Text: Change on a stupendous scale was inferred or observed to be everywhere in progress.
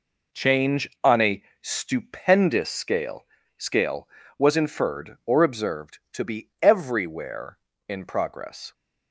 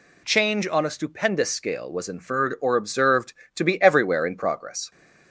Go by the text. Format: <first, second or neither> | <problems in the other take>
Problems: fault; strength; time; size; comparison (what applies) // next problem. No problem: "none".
second | pauses between "a" and "stupendous"; slight; at 1.4 s; 0.18 s long // says "scale" twice; at 3.5 s